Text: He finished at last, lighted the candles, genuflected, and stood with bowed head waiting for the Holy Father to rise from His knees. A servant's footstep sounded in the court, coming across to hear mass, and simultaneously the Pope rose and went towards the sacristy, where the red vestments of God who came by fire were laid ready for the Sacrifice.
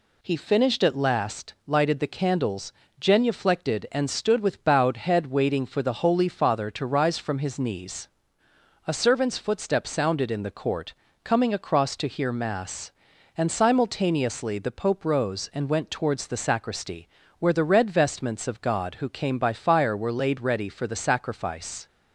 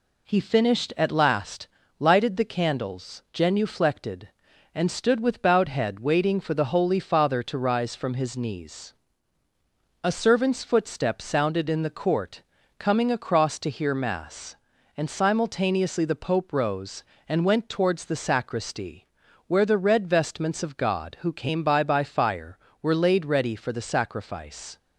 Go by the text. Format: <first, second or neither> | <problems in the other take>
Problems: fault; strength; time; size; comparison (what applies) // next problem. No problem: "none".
first | says "by" twice; at 21.8 s